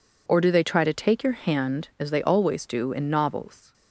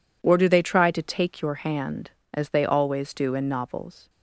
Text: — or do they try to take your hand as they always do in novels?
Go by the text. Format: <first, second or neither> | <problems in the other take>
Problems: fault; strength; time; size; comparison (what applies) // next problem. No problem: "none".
neither | none